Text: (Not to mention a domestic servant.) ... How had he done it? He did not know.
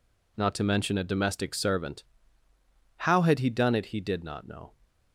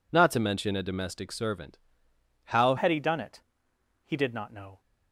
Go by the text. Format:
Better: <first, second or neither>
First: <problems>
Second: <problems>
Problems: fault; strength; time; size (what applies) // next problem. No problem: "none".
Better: first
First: none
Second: changes voice at "had"; from 2.7 s on; 2.0 s long